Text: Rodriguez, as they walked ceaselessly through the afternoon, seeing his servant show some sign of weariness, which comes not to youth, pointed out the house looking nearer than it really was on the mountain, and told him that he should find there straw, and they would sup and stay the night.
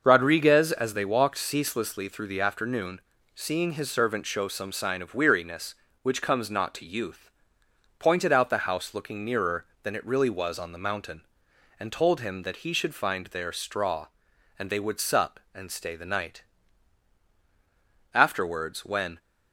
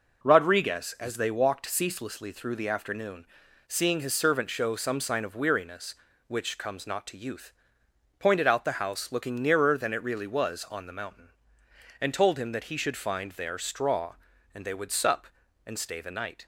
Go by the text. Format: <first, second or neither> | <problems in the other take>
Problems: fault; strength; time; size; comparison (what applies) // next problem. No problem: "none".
second | starts louder than the rest; until 1.0 s; 6 dB // goes on to say "Afterwards when"; noticeable; from 18.1 s on; 1.0 s long